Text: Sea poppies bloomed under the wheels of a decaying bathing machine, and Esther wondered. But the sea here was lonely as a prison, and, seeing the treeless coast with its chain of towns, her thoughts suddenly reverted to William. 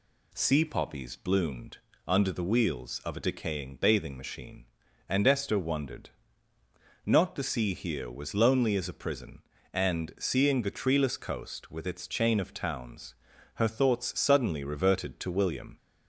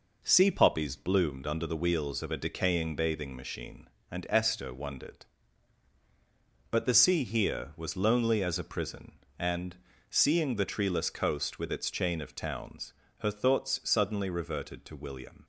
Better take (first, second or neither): second